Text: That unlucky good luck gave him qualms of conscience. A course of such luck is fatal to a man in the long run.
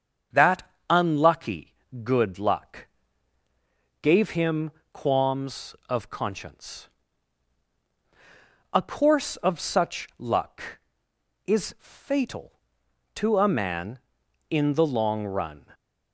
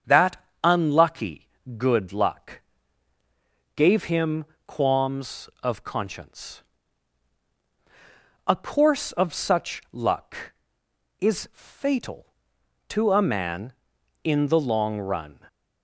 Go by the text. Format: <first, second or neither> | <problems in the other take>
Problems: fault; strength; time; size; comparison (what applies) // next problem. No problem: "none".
neither | starts louder than the rest; strong; the same in both // pauses between "That" and "unlucky"; slight; the same in both // pauses between "unlucky" and "good"; slight; the same in both // pauses between "luck" and "gave"; the same in both // pauses between "him" and "qualms"; slight; the same in both